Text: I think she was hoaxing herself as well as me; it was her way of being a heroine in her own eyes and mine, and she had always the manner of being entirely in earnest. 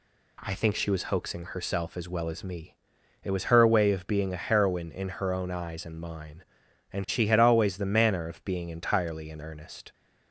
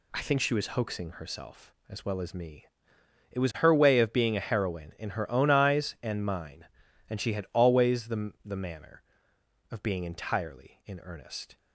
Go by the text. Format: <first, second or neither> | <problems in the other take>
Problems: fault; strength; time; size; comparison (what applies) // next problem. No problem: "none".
first | says "the" twice; at 8.4 s